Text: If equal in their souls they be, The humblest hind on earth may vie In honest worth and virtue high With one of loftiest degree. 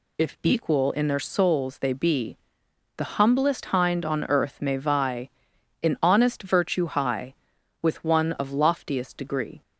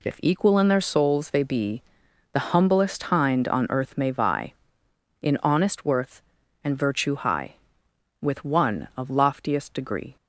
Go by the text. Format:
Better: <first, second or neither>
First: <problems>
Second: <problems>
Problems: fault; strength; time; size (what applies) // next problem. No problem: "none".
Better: second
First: skips "worth and"; at 6.4 s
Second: none